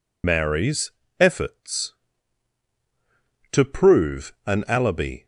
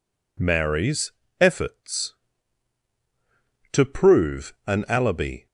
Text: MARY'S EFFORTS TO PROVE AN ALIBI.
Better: second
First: loses the start of "MARY'S"; at 0.2 s; 75 ms // pauses between "MARY'S" and "EFFORTS"; slight; at 0.8 s; 0.30 s long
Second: pauses between "MARY'S" and "EFFORTS"; slight; at 1.1 s; 0.30 s long

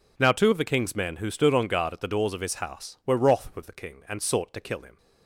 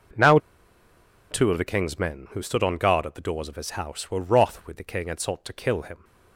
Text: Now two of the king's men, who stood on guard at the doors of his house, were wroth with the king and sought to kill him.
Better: first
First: none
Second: pauses between "Now" and "two"; noticeable; at 0.3 s; 0.93 s long

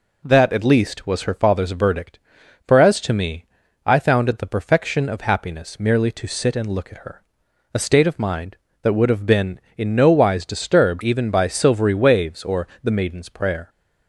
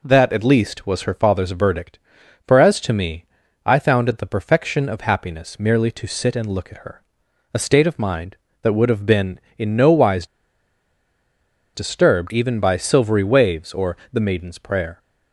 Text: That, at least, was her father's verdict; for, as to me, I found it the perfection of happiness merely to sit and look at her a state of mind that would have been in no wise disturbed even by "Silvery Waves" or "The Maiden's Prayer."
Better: first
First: pauses between "her" and "a"; noticeable; at 7.2 s; 0.52 s long // pauses between "or" and "The"; slight; at 12.6 s; 0.16 s long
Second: pauses between "her" and "a"; noticeable; at 7.0 s; 0.52 s long // pauses between "wise" and "disturbed"; strong; at 10.2 s; 1.4 s long // pauses between "or" and "The"; slight; at 13.9 s; 0.16 s long

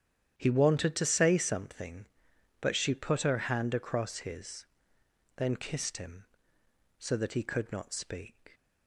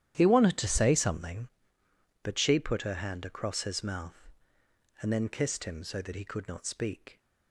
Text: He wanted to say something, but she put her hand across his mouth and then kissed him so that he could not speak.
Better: second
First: starts louder than the rest; strong; until 1.3 s; 10 dB // skips "mouth and"; at 5.0 s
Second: starts louder than the rest; strong; until 1.1 s; 11 dB

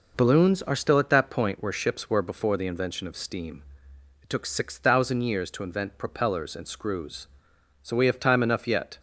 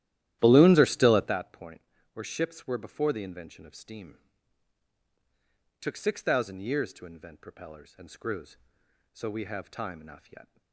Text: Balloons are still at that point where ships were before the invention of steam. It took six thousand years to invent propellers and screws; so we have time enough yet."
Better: first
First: none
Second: starts louder than the rest; strong; until 1.4 s; 14 dB // pauses between "point" and "where"; slight; at 1.8 s; 0.32 s long

